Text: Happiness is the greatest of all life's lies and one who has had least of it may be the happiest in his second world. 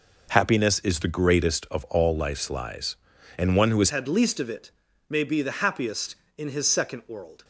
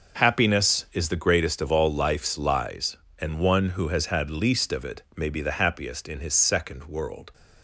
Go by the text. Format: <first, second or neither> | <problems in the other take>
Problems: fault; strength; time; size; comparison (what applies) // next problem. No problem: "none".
second | changes voice at "had"; from 3.8 s on; 3.6 s long // pauses between "it" and "may"; at 4.6 s; 0.40 s long